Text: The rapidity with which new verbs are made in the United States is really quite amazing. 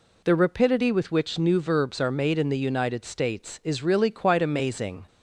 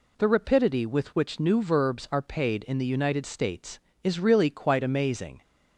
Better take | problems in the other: first | says "paid" for "made"; at 2.2 s

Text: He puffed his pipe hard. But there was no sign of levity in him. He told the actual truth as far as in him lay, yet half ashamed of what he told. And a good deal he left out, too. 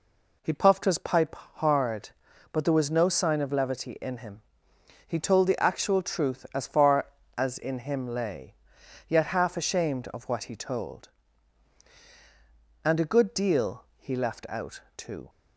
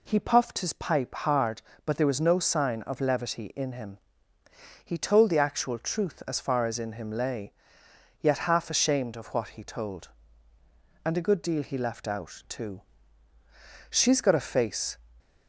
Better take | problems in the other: first | goes on to say "She's got a face"; noticeable; from 13.9 s on; 1.0 s long

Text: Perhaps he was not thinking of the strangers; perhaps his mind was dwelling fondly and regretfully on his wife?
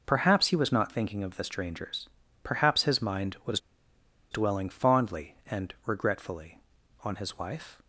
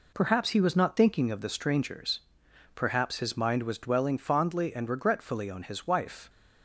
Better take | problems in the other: second | pauses between "was" and "dwelling"; noticeable; at 3.5 s; 0.73 s long

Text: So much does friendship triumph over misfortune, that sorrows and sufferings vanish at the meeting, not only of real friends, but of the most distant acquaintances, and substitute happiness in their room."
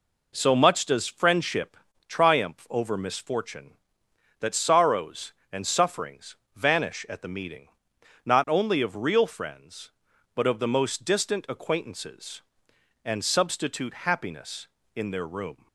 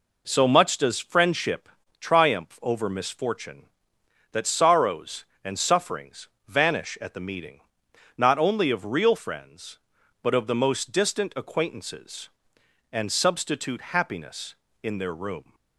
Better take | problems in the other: neither | pauses between "friendship" and "triumph"; slight; the same in both // pauses between "sufferings" and "vanish"; slight; the same in both

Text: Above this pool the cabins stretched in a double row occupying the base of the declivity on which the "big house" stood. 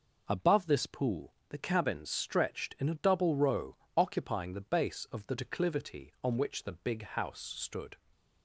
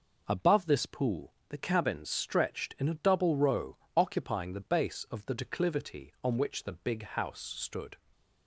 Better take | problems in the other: neither | pauses between "pool" and "the"; slight; the same in both // pauses between "row" and "occupying"; slight; the same in both

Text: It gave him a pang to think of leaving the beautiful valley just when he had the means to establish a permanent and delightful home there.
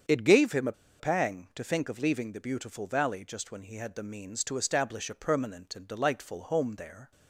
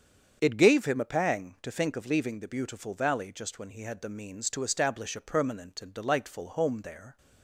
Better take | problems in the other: second | starts louder than the rest; strong; until 1.3 s; 7.5 dB; strong in the second // pauses between "a" and "pang"; slight; at 0.7 s; 0.27 s long

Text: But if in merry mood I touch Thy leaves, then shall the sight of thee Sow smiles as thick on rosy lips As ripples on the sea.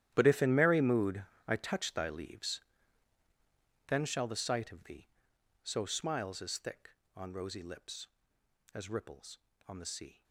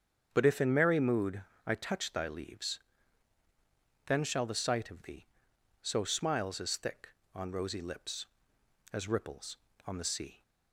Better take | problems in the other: second | gets quieter; strong; throughout; 16.5 dB // starts louder than the rest; strong; until 1.1 s; 12.5 dB; strong in the second // pauses between "mood" and "I"; slight; at 1.2 s; 0.24 s long; slight in the second // pauses between "thee" and "Sow"; noticeable; at 5.0 s; 0.56 s long; noticeable in the second

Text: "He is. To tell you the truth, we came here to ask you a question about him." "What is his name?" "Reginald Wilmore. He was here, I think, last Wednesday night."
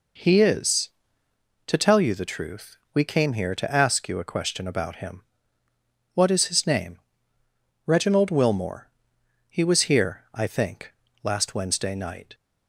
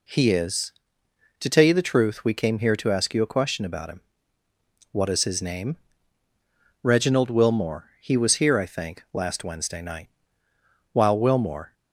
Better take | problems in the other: first | goes on to say "While Wilmore"; noticeable; from 10.9 s on; 0.80 s long

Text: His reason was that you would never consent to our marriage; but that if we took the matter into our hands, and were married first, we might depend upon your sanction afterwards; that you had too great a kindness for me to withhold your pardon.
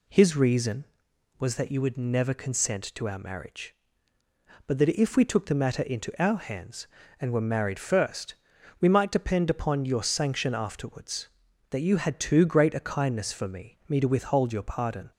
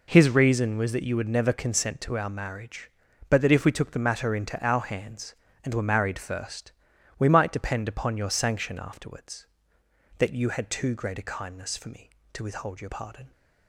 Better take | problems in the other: second | says "me" twice; at 13.8 s

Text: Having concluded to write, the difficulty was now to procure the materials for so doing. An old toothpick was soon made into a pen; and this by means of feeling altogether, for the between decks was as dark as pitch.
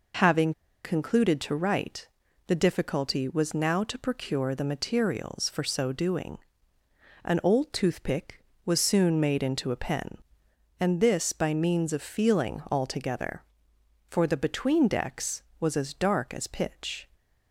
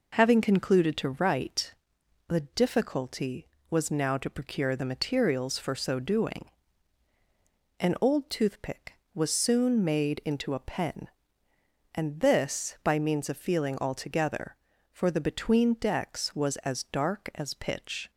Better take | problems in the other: second | pauses between "Having" and "concluded"; slight; at 0.5 s; 0.31 s long

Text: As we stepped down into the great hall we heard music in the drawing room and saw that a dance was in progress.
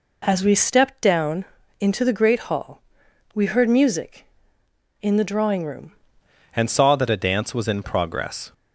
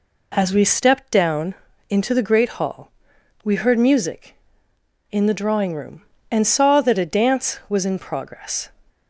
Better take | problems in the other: second | pauses between "down" and "into"; at 1.4 s; 0.38 s long; also in the second // pauses between "hall" and "we"; noticeable; at 2.8 s; 0.54 s long; noticeable in the second // changes voice at "and"; from 6.5 s on; 2.0 s long

